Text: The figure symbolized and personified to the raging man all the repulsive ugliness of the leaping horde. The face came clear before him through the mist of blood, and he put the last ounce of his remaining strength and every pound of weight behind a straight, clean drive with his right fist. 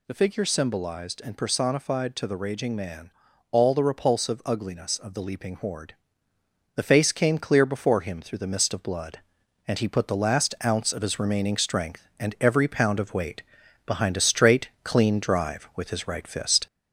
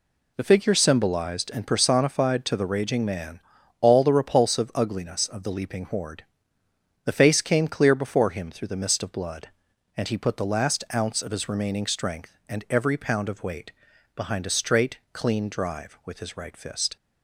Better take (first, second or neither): second